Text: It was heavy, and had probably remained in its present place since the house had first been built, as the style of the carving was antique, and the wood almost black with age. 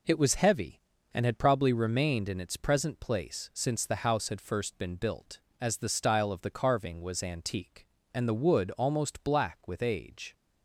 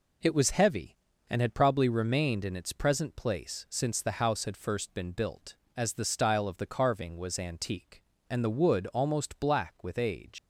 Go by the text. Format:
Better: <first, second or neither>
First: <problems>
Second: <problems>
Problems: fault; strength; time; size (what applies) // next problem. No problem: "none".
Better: first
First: none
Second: leaves "age" unfinished; at 10.3 s; 120 ms